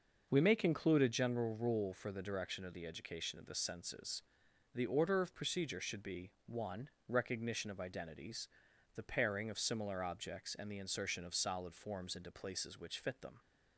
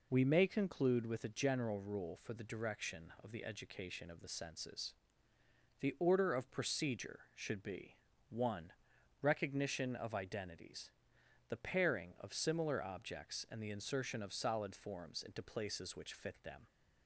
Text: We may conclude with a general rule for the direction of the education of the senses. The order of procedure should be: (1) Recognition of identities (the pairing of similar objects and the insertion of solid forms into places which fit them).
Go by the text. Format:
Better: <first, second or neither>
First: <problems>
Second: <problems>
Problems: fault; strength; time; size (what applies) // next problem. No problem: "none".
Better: second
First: starts louder than the rest; until 1.3 s; 6 dB // skips "with"; at 1.0 s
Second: none